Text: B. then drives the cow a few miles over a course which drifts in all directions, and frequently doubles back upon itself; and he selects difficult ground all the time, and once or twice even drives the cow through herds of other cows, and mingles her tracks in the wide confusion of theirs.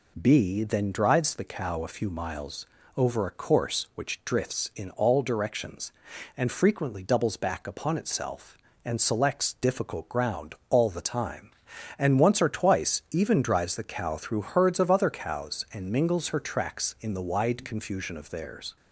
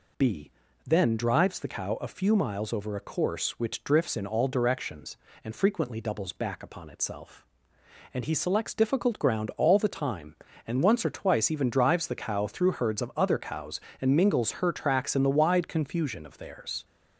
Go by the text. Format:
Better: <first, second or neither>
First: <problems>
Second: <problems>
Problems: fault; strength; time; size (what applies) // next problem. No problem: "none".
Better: second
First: pauses between "miles" and "over"; slight; at 2.6 s; 0.28 s long // skips "he"; at 8.9 s // pauses between "ground" and "all"; slight; at 10.5 s; 0.16 s long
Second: none